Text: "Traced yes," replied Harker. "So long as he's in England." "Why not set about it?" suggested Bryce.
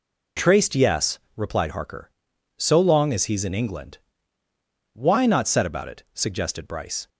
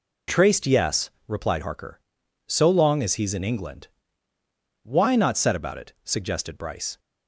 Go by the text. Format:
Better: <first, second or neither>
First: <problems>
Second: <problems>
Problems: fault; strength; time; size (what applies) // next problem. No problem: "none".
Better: neither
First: none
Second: none